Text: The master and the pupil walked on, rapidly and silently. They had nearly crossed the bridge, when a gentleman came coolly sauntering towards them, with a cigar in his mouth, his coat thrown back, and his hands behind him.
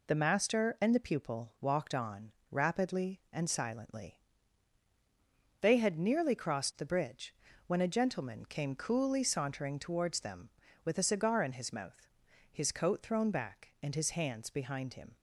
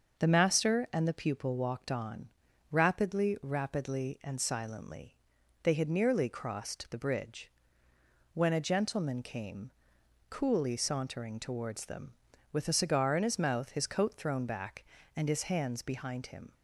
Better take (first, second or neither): first